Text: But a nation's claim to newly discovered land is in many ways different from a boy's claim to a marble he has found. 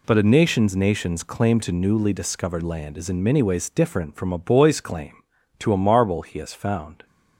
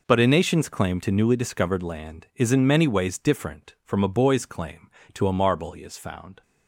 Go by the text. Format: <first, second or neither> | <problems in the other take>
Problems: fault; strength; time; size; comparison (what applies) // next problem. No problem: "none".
second | says "nation's" twice; at 0.7 s